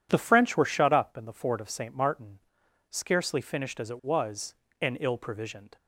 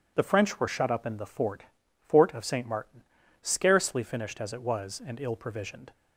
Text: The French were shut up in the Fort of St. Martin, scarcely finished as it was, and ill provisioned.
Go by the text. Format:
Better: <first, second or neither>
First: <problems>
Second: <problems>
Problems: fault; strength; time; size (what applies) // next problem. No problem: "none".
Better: first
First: none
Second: says "Fort" twice; at 2.0 s